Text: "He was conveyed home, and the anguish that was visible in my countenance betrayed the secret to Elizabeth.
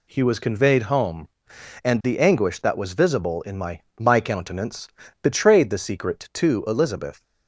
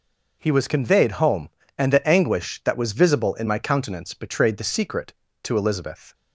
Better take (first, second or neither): second